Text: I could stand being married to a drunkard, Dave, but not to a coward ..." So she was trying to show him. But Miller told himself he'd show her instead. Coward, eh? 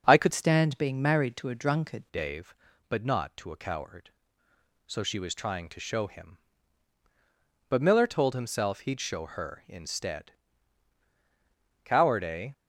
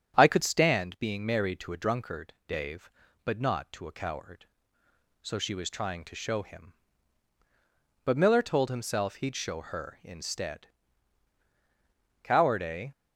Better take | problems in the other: second | starts louder than the rest; strong; until 1.0 s; 8.5 dB; strong in the second // changes voice from "stand" to "drunkard"; from 0.3 to 2.0 s; 1.7 s long

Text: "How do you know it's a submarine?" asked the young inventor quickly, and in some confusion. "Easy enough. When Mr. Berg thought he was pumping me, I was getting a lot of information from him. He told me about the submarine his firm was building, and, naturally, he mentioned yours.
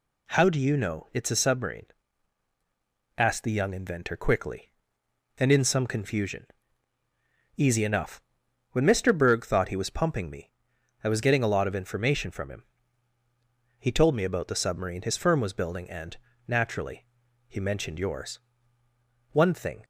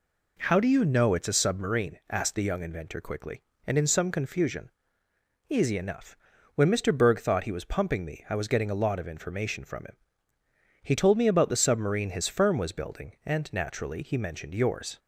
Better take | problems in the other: second | goes on to say "One thing"; from 19.3 s on; 0.52 s long

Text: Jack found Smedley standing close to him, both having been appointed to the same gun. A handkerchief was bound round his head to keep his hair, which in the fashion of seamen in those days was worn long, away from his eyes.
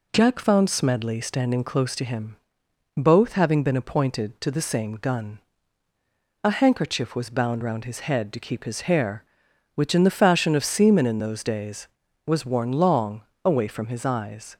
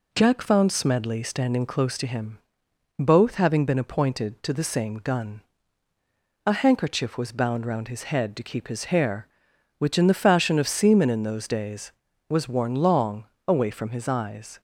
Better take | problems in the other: neither | none

